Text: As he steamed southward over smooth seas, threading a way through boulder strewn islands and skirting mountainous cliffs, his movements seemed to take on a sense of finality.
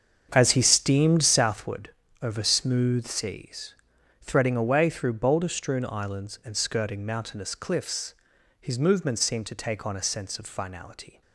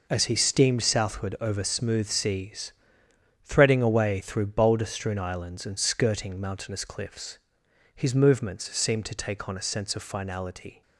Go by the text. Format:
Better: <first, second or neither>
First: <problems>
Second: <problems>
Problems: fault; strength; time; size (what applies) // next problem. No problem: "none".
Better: second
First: starts louder than the rest; strong; until 1.7 s; 7 dB // pauses between "southward" and "over"; slight; at 1.8 s; 0.32 s long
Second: none